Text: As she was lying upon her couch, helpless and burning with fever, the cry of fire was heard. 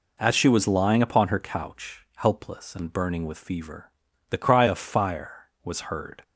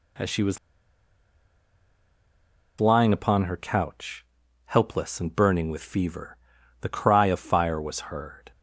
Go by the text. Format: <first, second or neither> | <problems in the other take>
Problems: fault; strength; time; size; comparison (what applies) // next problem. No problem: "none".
first | pauses between "was" and "lying"; strong; at 0.5 s; 2.2 s long